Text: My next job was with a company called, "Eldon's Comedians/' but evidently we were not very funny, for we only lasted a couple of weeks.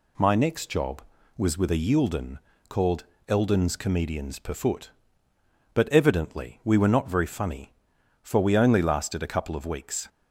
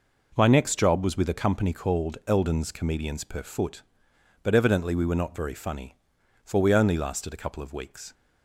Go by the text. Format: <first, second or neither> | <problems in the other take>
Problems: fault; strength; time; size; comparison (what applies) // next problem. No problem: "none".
second | says "yielden" for "company"; at 1.7 s